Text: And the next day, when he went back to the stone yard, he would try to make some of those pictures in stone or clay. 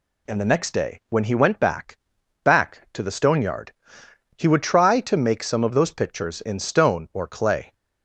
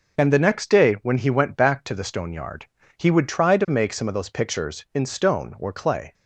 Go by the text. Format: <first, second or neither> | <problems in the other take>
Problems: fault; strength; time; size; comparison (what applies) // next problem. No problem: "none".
second | says "back" twice; at 2.4 s